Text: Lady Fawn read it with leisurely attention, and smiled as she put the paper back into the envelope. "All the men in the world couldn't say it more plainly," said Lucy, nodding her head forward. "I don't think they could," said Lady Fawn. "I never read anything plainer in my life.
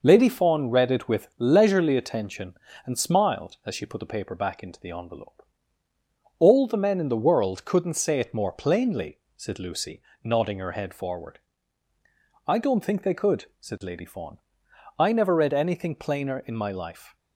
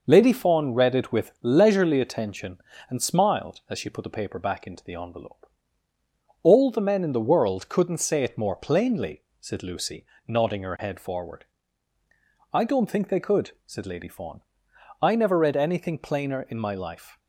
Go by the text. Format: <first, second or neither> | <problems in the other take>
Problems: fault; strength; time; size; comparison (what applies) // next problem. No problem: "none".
neither | none